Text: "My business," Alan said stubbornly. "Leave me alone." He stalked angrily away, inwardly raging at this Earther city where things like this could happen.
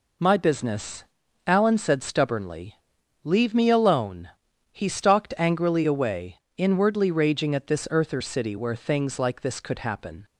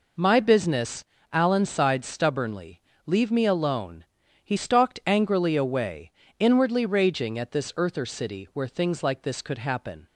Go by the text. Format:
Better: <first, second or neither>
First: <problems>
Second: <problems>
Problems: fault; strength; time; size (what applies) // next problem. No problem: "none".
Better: first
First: none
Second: says "sighed" for "said"; at 1.6 s